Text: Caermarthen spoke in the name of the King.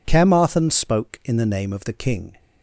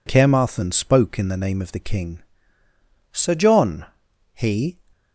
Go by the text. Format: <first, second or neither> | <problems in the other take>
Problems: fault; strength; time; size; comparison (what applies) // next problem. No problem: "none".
first | goes on to say "Sir John he"; from 3.1 s on; 1.6 s long